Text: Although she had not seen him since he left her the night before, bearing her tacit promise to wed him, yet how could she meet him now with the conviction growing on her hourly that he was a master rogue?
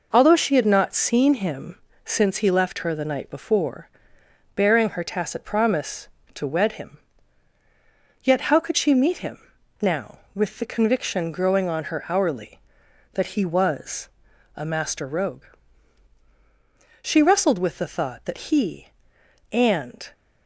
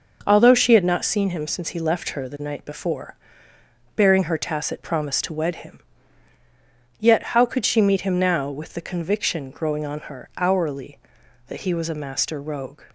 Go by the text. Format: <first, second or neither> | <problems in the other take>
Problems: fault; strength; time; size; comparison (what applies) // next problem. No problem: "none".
second | pauses between "him" and "since"; slight; at 1.7 s; 0.26 s long // pauses between "him" and "now"; at 9.3 s; 0.42 s long // pauses between "was" and "a"; noticeable; at 14.0 s; 0.46 s long // goes on to say "She wrestled with the thought that he and"; strong; from 17.0 s on; 3.0 s long